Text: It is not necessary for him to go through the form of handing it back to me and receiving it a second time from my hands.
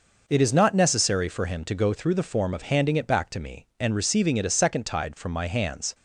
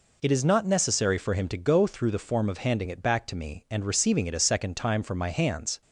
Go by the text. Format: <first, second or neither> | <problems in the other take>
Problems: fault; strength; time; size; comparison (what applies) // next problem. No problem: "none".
second | says "tide" for "time"; at 4.8 s